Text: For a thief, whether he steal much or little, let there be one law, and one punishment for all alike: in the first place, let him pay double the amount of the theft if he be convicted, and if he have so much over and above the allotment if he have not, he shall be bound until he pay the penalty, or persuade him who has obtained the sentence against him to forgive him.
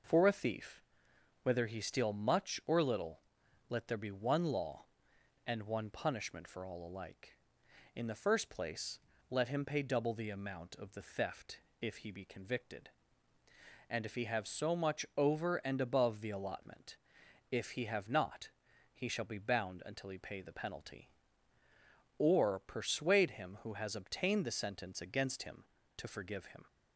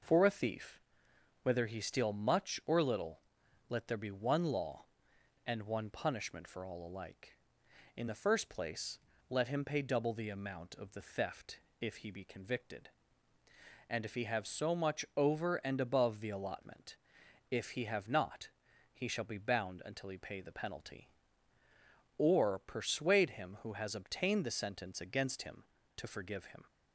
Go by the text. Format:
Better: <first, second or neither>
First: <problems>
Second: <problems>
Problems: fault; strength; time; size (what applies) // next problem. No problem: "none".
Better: neither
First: pauses between "theft" and "if"; slight; at 11.6 s; 0.20 s long // pauses between "allotment" and "if"; noticeable; at 16.9 s; 0.56 s long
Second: pauses between "theft" and "if"; slight; at 11.5 s; 0.20 s long // pauses between "allotment" and "if"; noticeable; at 16.9 s; 0.56 s long